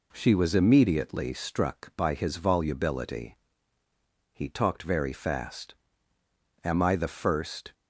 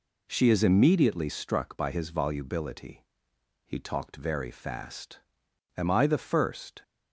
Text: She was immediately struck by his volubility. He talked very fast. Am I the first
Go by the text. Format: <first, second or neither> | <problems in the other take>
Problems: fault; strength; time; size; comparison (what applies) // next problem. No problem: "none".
first | says "is" for "was"; at 0.4 s